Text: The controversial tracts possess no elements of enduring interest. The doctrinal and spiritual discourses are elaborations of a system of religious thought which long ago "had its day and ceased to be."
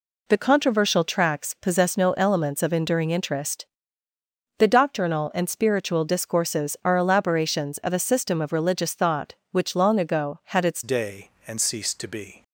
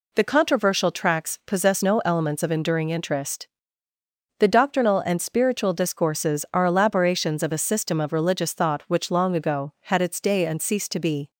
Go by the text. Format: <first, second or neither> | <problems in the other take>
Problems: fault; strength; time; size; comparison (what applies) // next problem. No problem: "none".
second | changes voice at "day"; from 10.8 s on; 1.6 s long